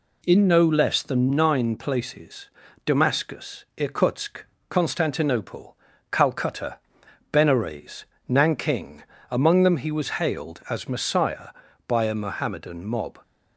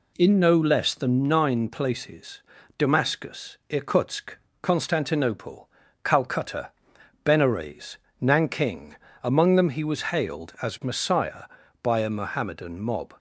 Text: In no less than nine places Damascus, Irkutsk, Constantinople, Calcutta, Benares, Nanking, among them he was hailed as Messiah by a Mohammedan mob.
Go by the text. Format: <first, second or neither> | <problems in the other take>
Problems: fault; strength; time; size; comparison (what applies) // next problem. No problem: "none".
neither | pauses between "places" and "Damascus"; the same in both